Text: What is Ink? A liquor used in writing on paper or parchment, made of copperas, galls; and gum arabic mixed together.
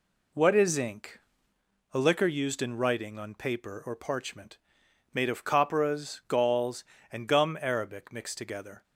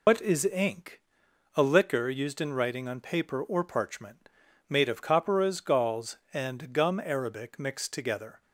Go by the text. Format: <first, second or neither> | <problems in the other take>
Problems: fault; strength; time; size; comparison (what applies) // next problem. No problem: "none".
first | loses the start of "What"; at 0.0 s; 140 ms